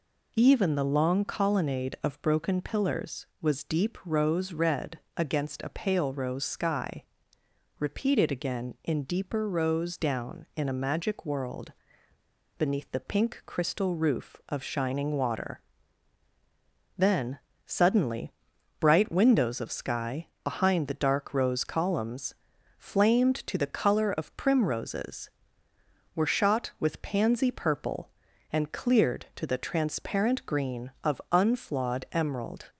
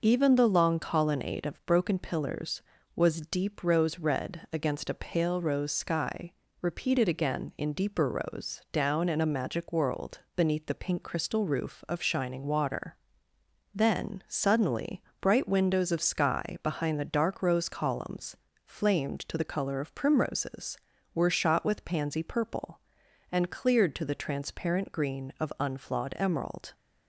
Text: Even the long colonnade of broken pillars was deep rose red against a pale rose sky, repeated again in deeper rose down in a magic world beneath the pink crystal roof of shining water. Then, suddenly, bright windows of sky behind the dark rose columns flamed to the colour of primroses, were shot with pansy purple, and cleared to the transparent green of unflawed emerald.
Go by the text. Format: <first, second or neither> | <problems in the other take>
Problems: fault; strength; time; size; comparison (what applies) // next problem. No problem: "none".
second | pauses between "red" and "against"; slight; at 4.9 s; 0.18 s long // pauses between "world" and "beneath"; noticeable; at 11.7 s; 0.84 s long // pauses between "sky" and "behind"; slight; at 20.2 s; 0.16 s long // pauses between "columns" and "flamed"; at 22.3 s; 0.44 s long; slight in the second